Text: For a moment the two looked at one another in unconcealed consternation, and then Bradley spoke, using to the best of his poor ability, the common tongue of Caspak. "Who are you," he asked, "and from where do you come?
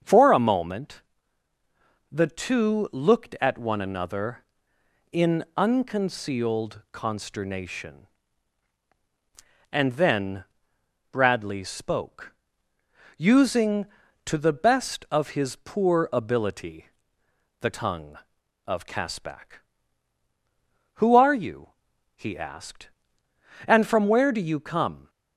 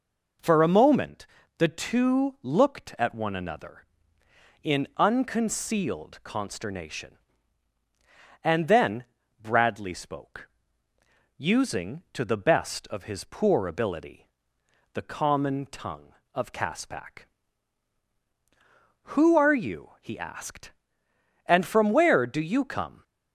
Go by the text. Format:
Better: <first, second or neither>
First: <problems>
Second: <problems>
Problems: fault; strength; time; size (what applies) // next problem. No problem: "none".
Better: second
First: starts louder than the rest; strong; until 2.1 s; 7.5 dB // pauses between "moment" and "the"; at 1.0 s; 1.1 s long // pauses between "then" and "Bradley"; noticeable; at 10.4 s; 0.68 s long // skips "common"; at 17.7 s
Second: pauses between "moment" and "the"; slight; at 1.2 s; 0.32 s long // pauses between "then" and "Bradley"; at 9.0 s; 0.38 s long